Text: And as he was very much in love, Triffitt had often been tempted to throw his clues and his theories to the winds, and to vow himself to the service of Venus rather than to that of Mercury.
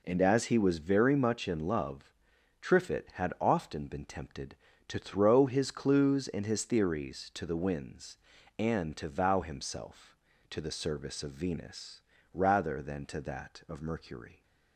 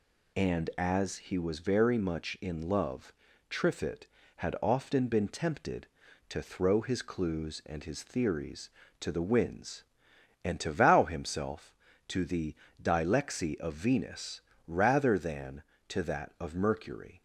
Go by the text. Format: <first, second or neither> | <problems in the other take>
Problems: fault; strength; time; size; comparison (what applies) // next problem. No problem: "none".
first | says "dilexi" for "service"; at 12.8 s // pauses between "Venus" and "rather"; slight; at 14.4 s; 0.26 s long; slight in the first